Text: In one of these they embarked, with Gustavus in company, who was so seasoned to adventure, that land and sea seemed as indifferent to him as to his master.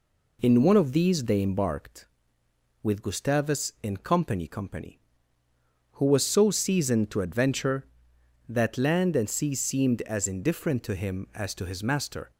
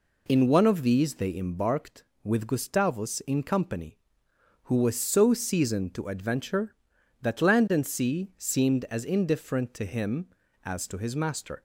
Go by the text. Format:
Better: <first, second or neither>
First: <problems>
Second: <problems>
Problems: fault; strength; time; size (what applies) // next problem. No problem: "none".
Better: second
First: says "company" twice; at 4.4 s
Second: none